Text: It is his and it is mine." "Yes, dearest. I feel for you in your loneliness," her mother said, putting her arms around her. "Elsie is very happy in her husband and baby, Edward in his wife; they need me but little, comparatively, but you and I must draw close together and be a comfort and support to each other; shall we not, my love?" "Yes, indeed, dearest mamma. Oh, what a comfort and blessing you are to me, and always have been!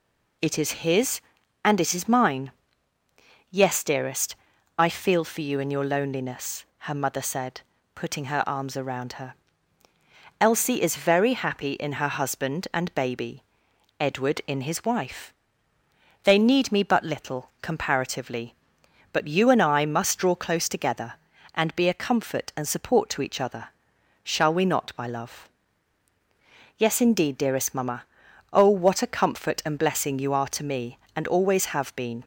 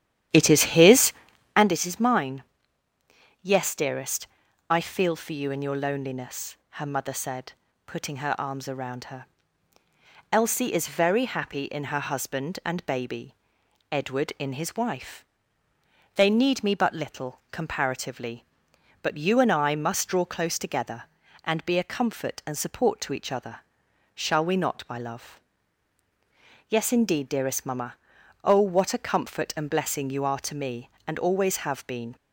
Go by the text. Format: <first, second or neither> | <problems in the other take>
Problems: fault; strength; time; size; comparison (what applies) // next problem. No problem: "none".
first | starts louder than the rest; strong; until 1.7 s; 11 dB